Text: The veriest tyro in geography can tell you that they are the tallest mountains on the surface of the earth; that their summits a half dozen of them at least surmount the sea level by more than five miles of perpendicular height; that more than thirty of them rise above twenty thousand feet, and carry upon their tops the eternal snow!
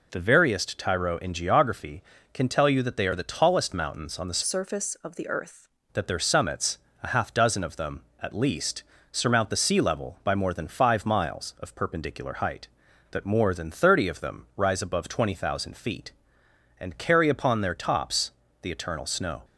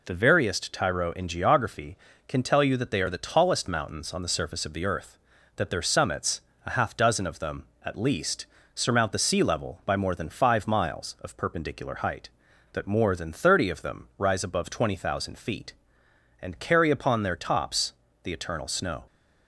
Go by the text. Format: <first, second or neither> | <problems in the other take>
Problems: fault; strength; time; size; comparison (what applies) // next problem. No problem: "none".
second | changes voice from "surface" to "earth"; from 4.4 to 5.6 s; 1.2 s long // pauses between "summits" and "a"; slight; at 6.7 s; 0.24 s long; slight in the second // pauses between "least" and "surmount"; slight; at 8.8 s; 0.30 s long; slight in the second // pauses between "tops" and "the"; slight; at 18.3 s; 0.32 s long; slight in the second